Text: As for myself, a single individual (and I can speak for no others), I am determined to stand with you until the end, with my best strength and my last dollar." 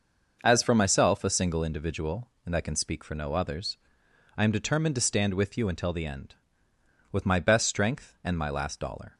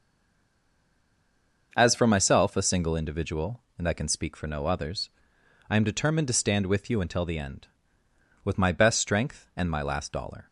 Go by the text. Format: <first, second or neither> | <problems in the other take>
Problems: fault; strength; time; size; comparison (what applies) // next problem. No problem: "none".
first | stays silent before the first word; noticeable; until 1.7 s; 1.7 s long // starts louder than the rest; noticeable; until 2.7 s; 6 dB; noticeable in the first